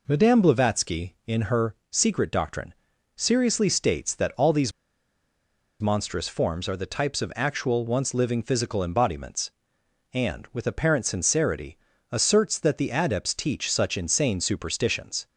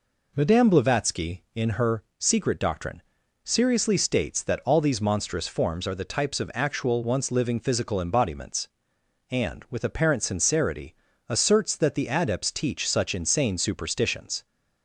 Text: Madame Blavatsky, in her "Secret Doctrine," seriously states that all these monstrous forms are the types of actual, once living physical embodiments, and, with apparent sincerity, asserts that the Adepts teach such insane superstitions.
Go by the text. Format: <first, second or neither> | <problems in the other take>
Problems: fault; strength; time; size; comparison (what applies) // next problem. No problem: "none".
second | pauses between "her" and "Secret"; slight; at 1.7 s; 0.16 s long; slight in the second // pauses between "these" and "monstrous"; at 4.7 s; 1.0 s long